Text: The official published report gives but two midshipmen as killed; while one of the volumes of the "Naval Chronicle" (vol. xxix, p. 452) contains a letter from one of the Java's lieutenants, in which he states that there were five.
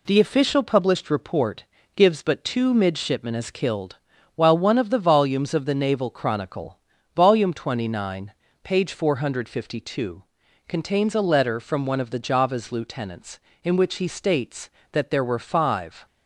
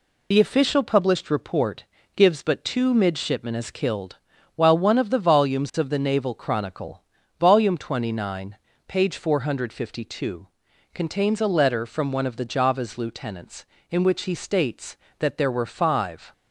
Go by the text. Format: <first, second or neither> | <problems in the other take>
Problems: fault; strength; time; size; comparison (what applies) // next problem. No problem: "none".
first | loses the start of "The"; at 0.3 s; 40 ms // pauses between "report" and "gives"; slight; at 1.8 s; 0.32 s long; slight in the first